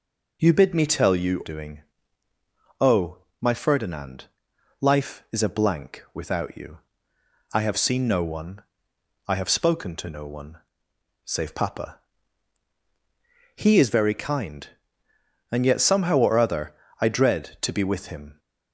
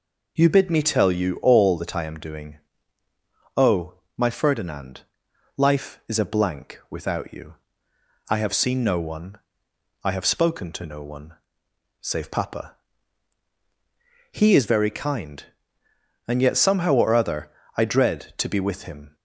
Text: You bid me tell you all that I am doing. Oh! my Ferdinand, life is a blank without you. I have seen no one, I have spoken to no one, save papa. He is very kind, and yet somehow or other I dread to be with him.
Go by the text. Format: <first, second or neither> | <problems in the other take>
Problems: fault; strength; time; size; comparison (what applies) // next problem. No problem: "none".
second | skips "all that I am"; at 1.4 s // pauses between "other" and "I"; slight; at 16.7 s; 0.28 s long; slight in the second